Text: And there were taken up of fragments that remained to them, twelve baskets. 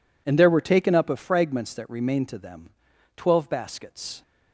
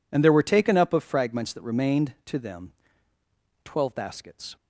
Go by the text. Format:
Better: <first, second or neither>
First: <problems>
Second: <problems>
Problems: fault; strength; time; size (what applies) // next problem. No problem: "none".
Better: neither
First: none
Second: none